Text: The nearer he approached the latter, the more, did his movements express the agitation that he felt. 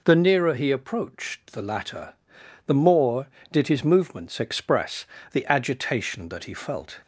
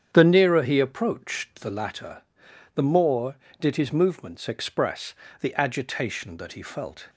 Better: first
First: pauses between "express" and "the"; slight; at 5.0 s; 0.26 s long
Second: starts louder than the rest; strong; until 1.9 s; 8.5 dB // pauses between "express" and "the"; slight; at 5.1 s; 0.26 s long

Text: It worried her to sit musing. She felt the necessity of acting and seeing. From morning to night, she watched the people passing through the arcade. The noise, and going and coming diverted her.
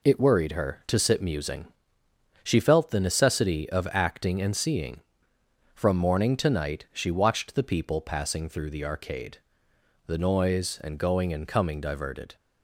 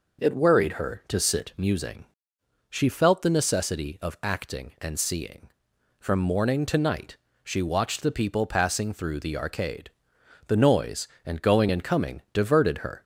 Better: second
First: stops before "her"; at 12.3 s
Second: none

